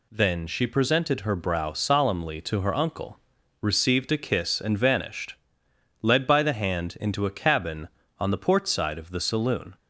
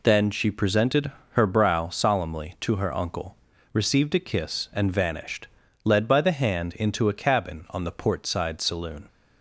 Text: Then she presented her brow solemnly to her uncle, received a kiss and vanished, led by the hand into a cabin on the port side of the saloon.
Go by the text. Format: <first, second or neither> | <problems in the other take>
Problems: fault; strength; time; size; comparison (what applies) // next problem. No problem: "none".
first | pauses between "presented" and "her"; slight; at 1.1 s; 0.20 s long // skips "of the"; at 8.6 s